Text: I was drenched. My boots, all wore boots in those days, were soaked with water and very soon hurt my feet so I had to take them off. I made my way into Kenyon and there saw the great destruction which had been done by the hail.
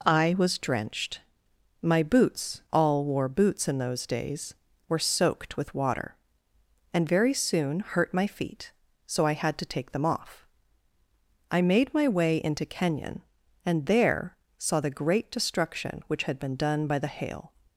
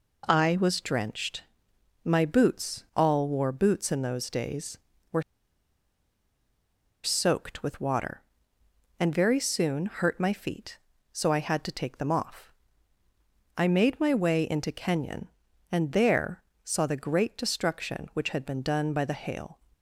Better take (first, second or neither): first